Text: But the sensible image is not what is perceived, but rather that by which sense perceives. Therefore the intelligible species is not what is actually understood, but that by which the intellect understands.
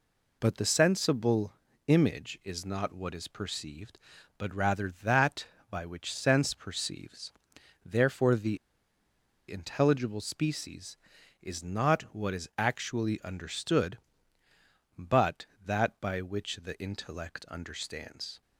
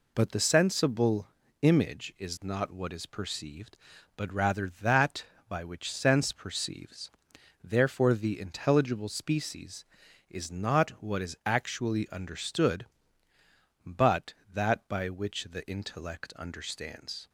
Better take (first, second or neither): second